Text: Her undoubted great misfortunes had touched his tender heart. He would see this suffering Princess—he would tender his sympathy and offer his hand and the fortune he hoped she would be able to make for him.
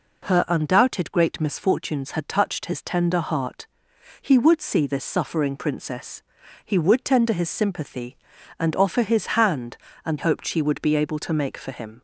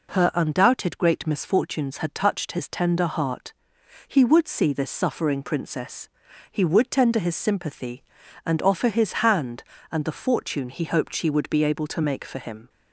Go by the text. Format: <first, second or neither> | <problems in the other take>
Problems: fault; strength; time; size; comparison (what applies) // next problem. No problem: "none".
second | skips "the fortune he"; at 10.1 s